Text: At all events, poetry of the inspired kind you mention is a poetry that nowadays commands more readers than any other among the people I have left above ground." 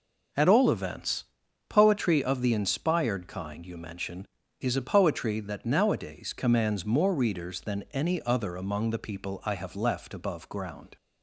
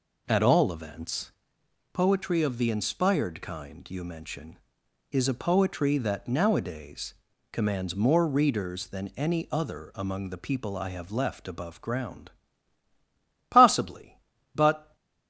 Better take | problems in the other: first | pauses between "nowadays" and "commands"; at 7.1 s; 0.38 s long // goes on to say "Possibly but"; from 13.5 s on; 1.4 s long

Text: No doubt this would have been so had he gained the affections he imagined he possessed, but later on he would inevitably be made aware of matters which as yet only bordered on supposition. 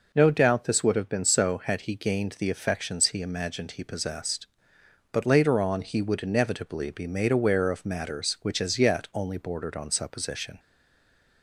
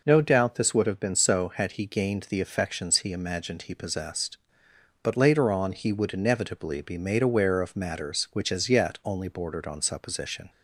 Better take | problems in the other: second | stays silent after the last word; slight; from 10.5 s on; 0.9 s long

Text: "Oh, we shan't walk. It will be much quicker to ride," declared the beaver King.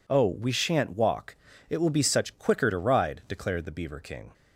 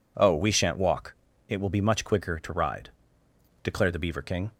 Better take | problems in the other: second | says "such" for "much"; at 2.0 s

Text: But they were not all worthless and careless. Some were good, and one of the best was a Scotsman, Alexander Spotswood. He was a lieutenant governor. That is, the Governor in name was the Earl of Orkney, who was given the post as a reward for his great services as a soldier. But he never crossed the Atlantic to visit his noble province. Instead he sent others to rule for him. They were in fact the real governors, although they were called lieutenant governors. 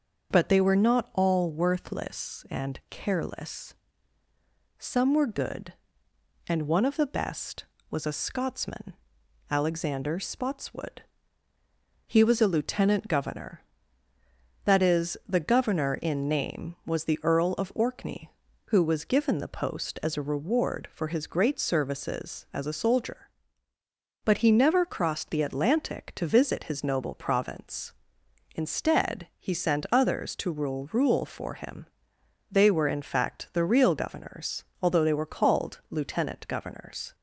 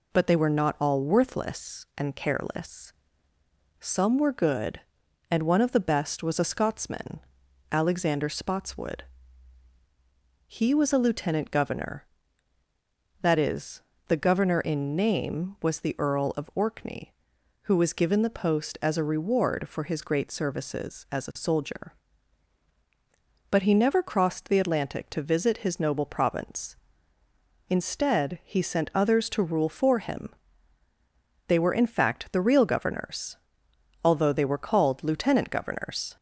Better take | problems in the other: second | starts louder than the rest; until 1.3 s; 6.5 dB // says "rule" twice; at 30.9 s

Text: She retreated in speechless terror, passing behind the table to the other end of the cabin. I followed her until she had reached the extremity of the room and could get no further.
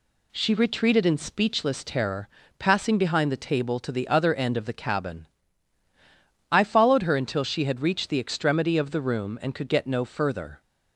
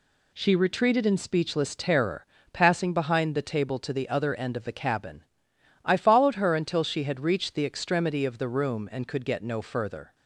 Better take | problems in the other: neither | none

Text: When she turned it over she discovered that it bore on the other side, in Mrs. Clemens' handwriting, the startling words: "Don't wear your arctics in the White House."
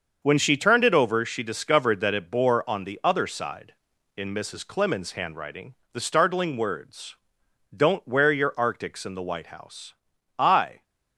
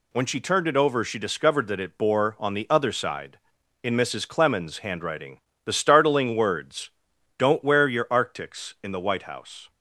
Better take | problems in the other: second | starts louder than the rest; until 1.2 s; 6.5 dB // goes on to say "I"; slight; from 10.3 s on; 0.44 s long

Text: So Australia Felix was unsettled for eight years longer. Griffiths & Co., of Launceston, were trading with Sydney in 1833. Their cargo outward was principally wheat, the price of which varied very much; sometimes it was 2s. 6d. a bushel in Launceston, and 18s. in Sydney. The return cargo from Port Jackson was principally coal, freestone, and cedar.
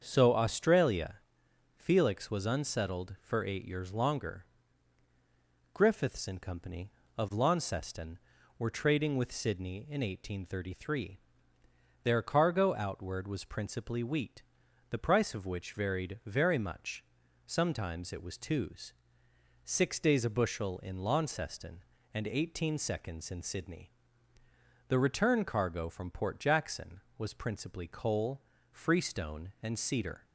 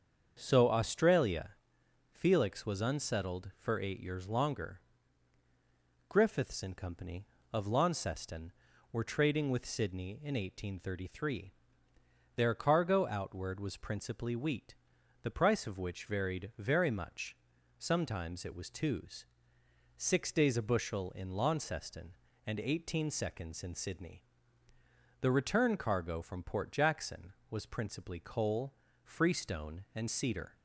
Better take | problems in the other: neither | starts louder than the rest; strong; the same in both // pauses between "Australia" and "Felix"; noticeable; the same in both

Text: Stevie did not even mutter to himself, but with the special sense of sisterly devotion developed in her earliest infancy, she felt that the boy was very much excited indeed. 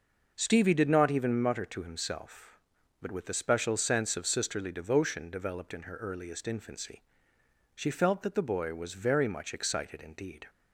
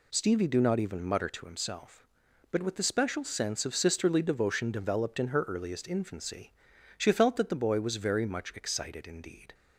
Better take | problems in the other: first | says "do" for "did"; at 0.4 s

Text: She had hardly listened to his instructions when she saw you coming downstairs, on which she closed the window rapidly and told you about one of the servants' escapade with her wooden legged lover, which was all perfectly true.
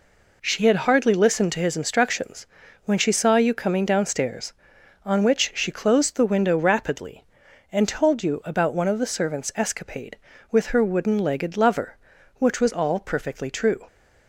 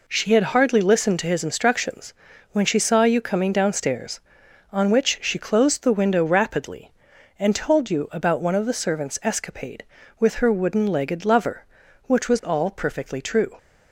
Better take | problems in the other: neither | pauses between "instructions" and "when"; the same in both

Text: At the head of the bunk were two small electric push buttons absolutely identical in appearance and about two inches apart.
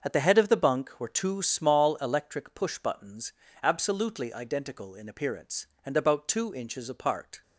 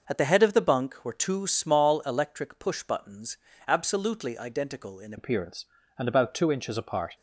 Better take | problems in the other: first | starts louder than the rest; noticeable; until 1.0 s; 6 dB; also in the first // pauses between "buttons" and "absolutely"; slight; at 3.3 s; 0.30 s long; slight in the first // changes voice at "appearance"; from 5.1 s on; 2.0 s long

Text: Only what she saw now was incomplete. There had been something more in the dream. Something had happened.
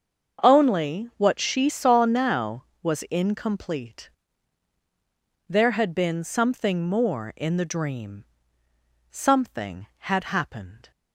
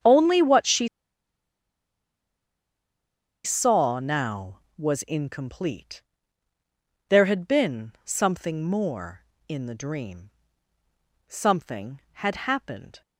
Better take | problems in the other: first | starts louder than the rest; strong; until 3.6 s; 7.5 dB; also in the first // pauses between "she" and "saw"; strong; at 0.8 s; 2.5 s long

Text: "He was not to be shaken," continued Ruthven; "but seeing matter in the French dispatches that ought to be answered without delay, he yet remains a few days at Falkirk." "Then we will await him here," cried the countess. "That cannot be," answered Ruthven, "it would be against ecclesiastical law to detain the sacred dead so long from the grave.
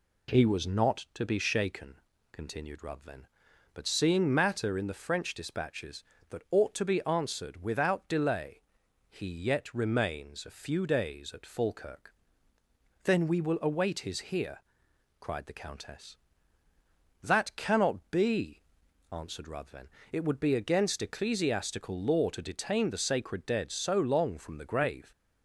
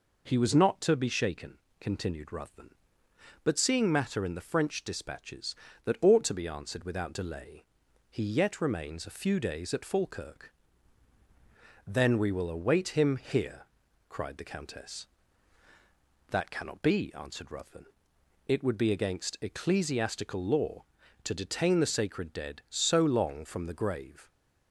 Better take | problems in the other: second | says "his" for "him"; at 14.0 s

